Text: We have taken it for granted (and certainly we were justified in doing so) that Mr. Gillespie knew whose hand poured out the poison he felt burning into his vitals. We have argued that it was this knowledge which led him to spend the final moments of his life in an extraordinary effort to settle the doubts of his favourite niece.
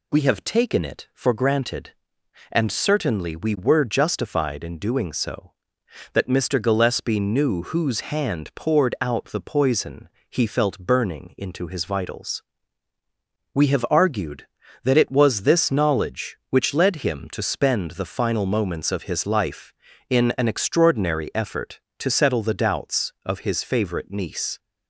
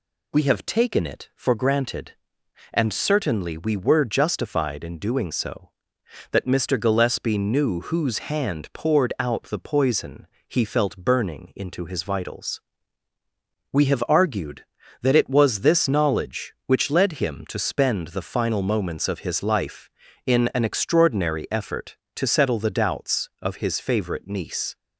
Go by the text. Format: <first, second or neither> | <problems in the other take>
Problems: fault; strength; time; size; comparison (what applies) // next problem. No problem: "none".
neither | pauses between "poison" and "he"; slight; the same in both